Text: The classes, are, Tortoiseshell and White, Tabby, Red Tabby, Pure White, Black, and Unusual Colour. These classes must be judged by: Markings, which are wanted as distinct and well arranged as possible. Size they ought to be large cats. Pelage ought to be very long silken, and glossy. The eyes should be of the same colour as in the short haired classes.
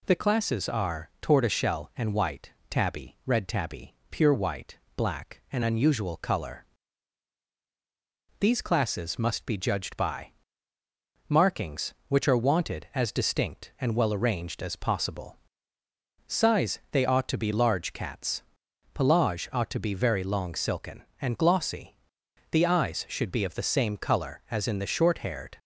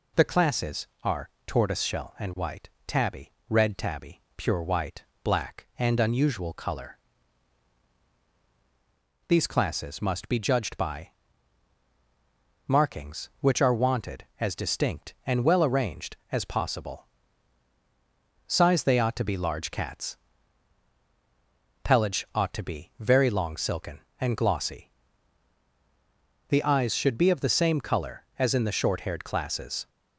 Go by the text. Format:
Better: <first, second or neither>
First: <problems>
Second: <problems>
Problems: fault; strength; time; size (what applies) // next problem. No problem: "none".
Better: second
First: stops before "classes"; at 25.5 s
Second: none